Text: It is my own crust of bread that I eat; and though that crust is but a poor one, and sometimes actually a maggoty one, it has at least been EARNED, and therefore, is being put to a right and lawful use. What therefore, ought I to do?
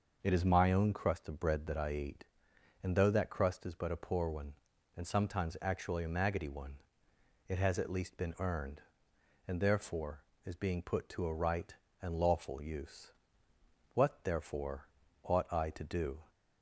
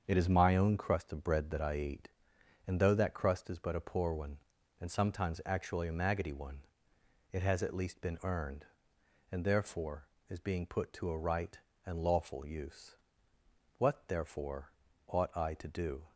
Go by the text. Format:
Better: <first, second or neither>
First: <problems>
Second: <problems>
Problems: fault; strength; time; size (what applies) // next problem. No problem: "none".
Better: first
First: starts louder than the rest; noticeable; until 1.2 s; 6 dB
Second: gets quieter; throughout; 6.5 dB // starts louder than the rest; until 1.0 s; 7 dB